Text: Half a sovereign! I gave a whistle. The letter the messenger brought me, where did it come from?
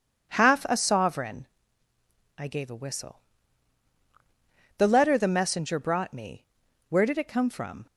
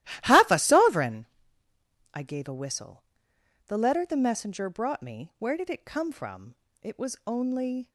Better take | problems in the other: first | starts louder than the rest; strong; until 1.2 s; 14.5 dB // goes on to say "It was only"; noticeable; from 6.8 s on; 1.0 s long

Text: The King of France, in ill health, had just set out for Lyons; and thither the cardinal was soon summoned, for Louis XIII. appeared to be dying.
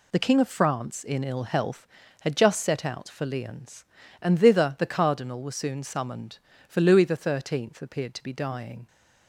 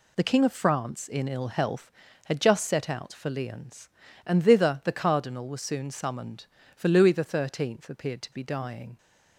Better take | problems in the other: neither | none

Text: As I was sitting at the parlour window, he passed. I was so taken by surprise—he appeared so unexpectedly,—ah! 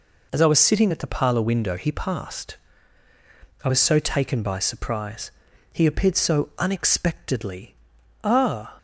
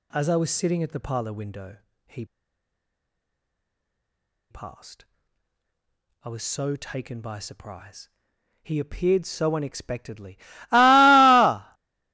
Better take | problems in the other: first | pauses between "he" and "passed"; strong; at 2.2 s; 2.2 s long

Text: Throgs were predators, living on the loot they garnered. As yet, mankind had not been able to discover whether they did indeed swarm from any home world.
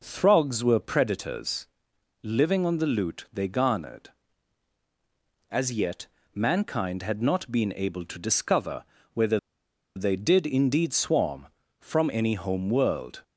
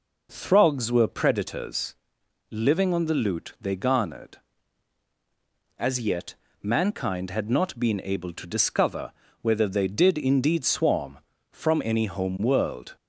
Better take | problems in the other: second | pauses between "discover" and "whether"; slight; at 8.8 s; 0.30 s long; slight in the second // pauses between "whether" and "they"; noticeable; at 9.3 s; 0.57 s long

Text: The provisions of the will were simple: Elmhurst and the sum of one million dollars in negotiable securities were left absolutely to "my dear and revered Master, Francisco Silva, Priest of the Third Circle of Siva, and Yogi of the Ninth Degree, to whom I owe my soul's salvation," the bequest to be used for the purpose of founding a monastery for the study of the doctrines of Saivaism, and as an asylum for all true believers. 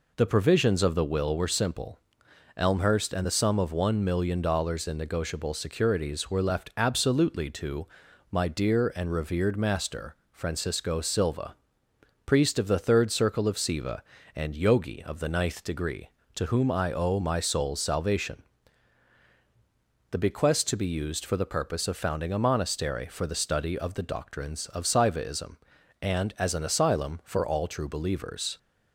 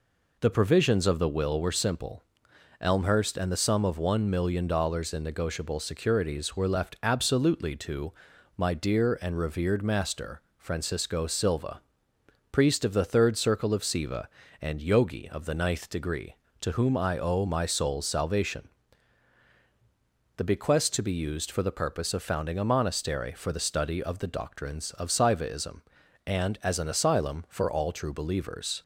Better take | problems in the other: neither | pauses between "to" and "my"; the same in both

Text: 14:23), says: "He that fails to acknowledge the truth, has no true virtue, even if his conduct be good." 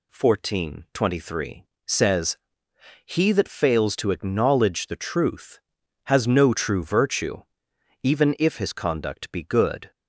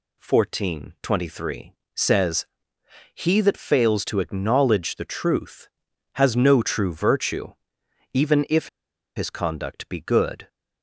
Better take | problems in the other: first | pauses between "if" and "his"; noticeable; at 8.6 s; 0.49 s long

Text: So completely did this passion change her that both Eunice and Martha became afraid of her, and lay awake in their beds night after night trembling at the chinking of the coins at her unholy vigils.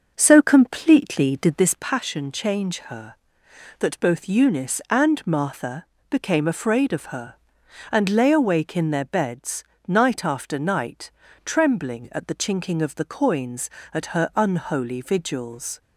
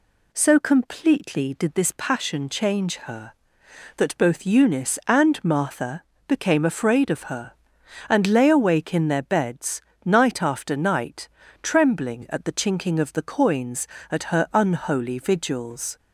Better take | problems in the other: second | starts louder than the rest; noticeable; until 1.9 s; 6 dB // pauses between "Martha" and "became"; slight; at 5.8 s; 0.26 s long; slight in the second // pauses between "beds" and "night"; slight; at 9.6 s; 0.24 s long; slight in the second // pauses between "night" and "trembling"; slight; at 11.1 s; 0.34 s long; slight in the second

